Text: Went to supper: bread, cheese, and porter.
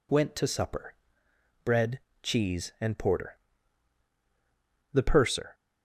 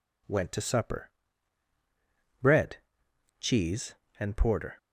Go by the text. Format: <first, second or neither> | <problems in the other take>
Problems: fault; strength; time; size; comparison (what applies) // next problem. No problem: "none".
second | goes on to say "The purser"; noticeable; from 4.9 s on; 0.62 s long